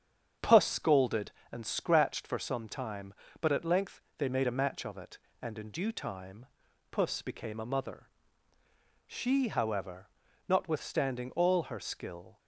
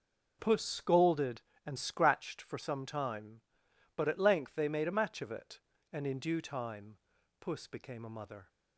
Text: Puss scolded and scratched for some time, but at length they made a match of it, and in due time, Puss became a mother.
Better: second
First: starts louder than the rest; strong; until 1.6 s; 8 dB // pauses between "length" and "they"; slight; at 4.0 s; 0.16 s long // goes on to say "She however notwithstanding all her skill"; strong; from 9.0 s on; 3.3 s long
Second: none

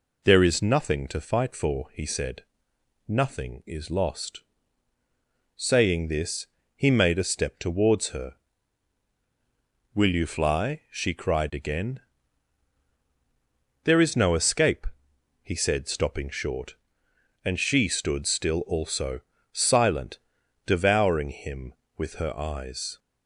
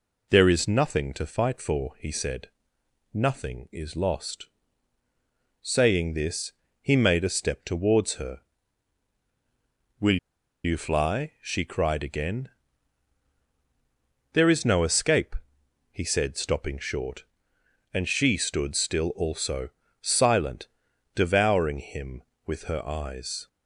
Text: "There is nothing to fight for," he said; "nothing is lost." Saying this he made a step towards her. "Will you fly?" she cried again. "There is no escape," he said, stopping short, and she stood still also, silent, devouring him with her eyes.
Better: first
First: pauses between "this" and "he"; slight; at 6.4 s; 0.30 s long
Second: pauses between "this" and "he"; slight; at 6.5 s; 0.30 s long // pauses between "Will" and "you"; noticeable; at 10.1 s; 0.46 s long

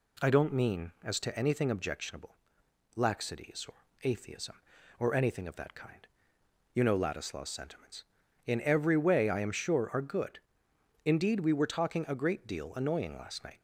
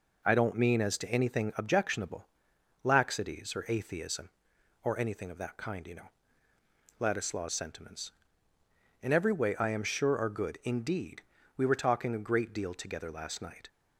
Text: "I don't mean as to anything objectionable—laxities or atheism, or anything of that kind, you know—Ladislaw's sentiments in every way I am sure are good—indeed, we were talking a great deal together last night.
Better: second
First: pauses between "or" and "atheism"; slight; at 3.8 s; 0.18 s long // says "annoying" for "together"; at 12.7 s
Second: none

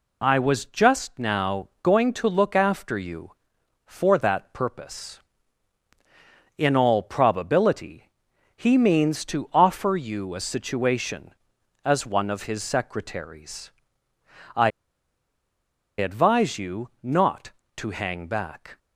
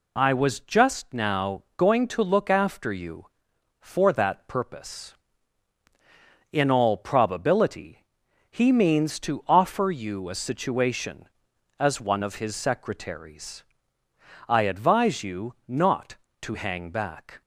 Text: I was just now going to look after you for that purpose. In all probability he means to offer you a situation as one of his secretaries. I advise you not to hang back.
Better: second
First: pauses between "now" and "going"; slight; at 1.6 s; 0.16 s long // pauses between "probability" and "he"; noticeable; at 8.0 s; 0.46 s long // pauses between "I" and "advise"; strong; at 14.6 s; 1.2 s long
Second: pauses between "now" and "going"; slight; at 1.6 s; 0.16 s long // pauses between "probability" and "he"; noticeable; at 8.0 s; 0.46 s long

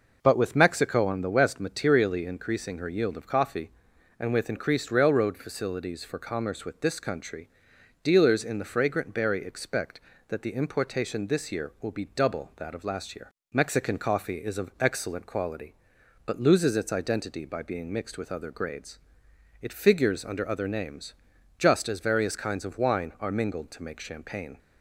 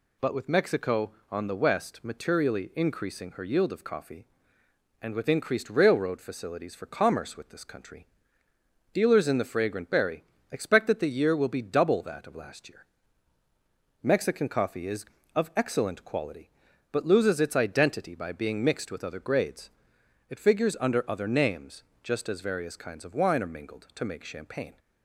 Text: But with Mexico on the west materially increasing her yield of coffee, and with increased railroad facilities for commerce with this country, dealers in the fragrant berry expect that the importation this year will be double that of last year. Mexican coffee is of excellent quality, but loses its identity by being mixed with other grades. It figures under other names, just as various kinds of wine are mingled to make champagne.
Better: first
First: none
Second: pauses between "berry" and "expect"; slight; at 10.2 s; 0.26 s long // skips "importation this"; at 11.0 s

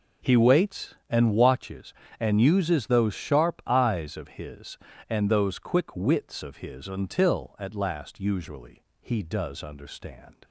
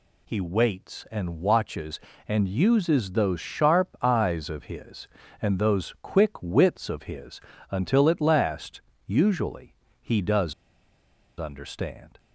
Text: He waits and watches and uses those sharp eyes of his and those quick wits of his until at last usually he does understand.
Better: first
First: pauses between "usually" and "he"; slight; at 8.8 s; 0.18 s long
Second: pauses between "his" and "until"; slight; at 7.4 s; 0.30 s long // pauses between "last" and "usually"; slight; at 8.8 s; 0.26 s long // pauses between "usually" and "he"; slight; at 9.7 s; 0.26 s long // pauses between "does" and "understand"; noticeable; at 10.5 s; 0.86 s long

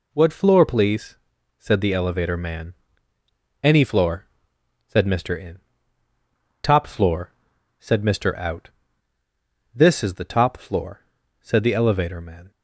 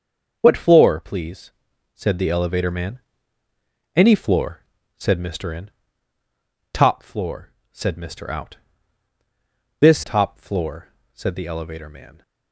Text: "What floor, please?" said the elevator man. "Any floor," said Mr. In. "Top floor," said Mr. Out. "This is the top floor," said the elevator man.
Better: first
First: none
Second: starts louder than the rest; until 1.4 s; 6.5 dB // skips "is the"; at 10.0 s

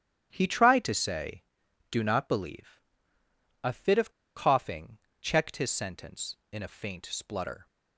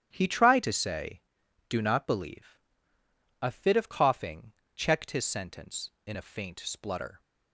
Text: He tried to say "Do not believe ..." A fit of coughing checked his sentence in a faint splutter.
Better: second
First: starts louder than the rest; until 1.3 s; 7 dB // pauses between "of" and "coughing"; slight; at 4.1 s; 0.24 s long // pauses between "coughing" and "checked"; slight; at 5.0 s; 0.20 s long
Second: starts louder than the rest; strong; until 1.1 s; 7 dB // pauses between "coughing" and "checked"; slight; at 4.5 s; 0.20 s long

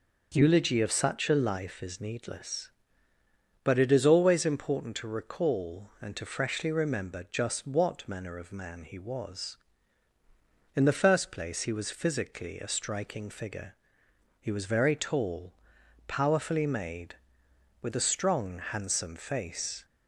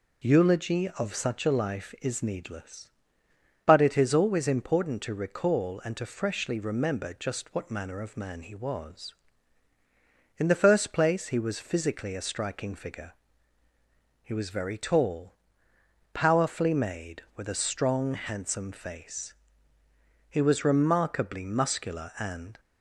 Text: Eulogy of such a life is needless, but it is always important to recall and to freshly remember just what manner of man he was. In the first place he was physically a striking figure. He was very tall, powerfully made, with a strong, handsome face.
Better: first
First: none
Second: goes on to say "He was remarkably muscular and"; strong; from 20.2 s on; 2.3 s long

